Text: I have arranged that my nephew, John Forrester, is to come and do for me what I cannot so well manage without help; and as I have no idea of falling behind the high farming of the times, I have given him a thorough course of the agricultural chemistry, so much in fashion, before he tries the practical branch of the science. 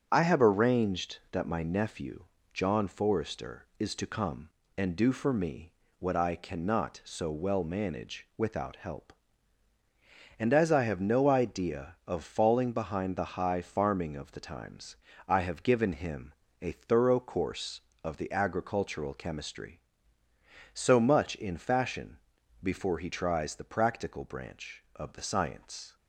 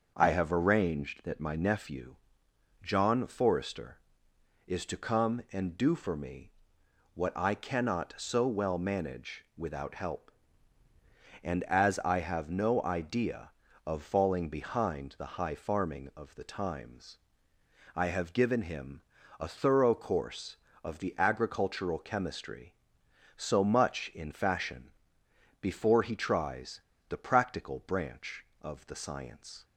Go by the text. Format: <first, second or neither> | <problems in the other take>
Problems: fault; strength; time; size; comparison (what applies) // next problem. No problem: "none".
first | starts louder than the rest; until 1.1 s; 6.5 dB; strong in the first // pauses between "me" and "what"; noticeable; at 6.5 s; 0.64 s long; slight in the first // pauses between "him" and "a"; at 19.0 s; 0.38 s long; slight in the first // pauses between "tries" and "the"; slight; at 26.8 s; 0.26 s long